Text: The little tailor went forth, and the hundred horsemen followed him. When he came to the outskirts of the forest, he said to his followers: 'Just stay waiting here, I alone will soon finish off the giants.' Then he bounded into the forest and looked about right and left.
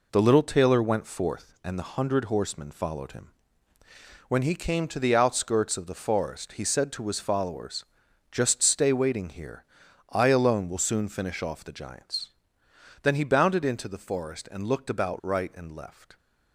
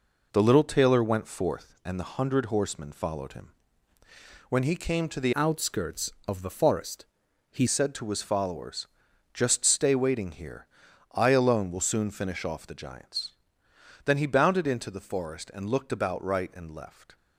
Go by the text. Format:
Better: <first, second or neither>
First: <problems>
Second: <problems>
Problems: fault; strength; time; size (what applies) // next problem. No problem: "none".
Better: first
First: none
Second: changes voice from "outskirts" to "he"; from 5.3 to 7.6 s; 2.3 s long